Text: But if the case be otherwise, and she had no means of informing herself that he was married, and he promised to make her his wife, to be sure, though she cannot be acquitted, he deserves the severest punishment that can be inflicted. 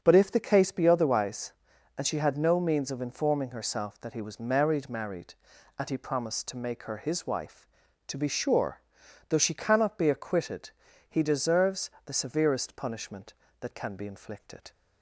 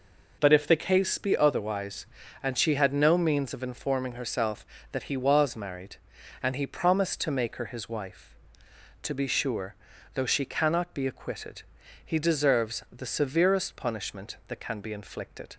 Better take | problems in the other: second | starts louder than the rest; until 1.0 s; 7 dB // says "married" twice; at 4.8 s // pauses between "deserves" and "the"; slight; at 11.9 s; 0.16 s long

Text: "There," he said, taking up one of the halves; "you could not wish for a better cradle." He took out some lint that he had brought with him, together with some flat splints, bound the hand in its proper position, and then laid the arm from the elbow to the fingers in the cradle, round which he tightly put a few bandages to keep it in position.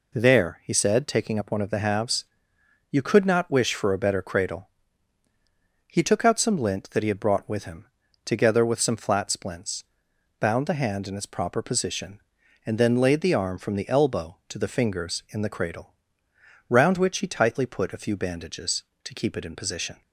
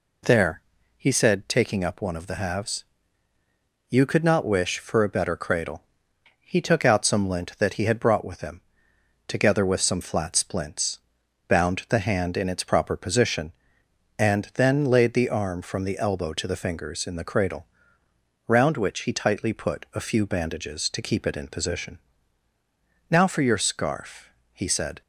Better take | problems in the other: first | goes on to say "Now for your scarf he said"; strong; from 23.1 s on; 1.9 s long

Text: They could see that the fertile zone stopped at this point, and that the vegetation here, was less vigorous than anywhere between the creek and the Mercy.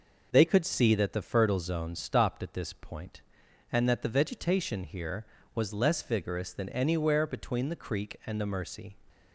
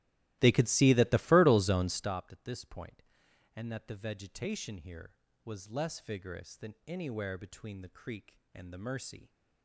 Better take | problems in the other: first | starts louder than the rest; strong; until 2.1 s; 16 dB

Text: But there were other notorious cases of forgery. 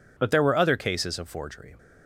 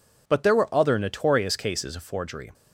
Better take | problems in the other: second | skips "notorious"; at 0.7 s

